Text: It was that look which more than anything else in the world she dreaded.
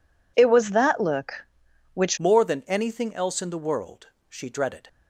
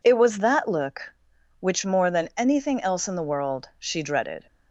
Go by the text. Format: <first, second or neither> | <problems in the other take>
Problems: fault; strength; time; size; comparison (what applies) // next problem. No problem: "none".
second | changes voice at "more"; from 2.1 s on; 2.7 s long // pauses between "world" and "she"; slight; at 4.0 s; 0.22 s long